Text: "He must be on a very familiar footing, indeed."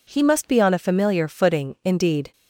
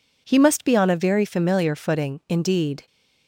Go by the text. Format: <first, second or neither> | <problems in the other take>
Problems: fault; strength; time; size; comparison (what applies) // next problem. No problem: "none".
second | skips "very"; at 0.7 s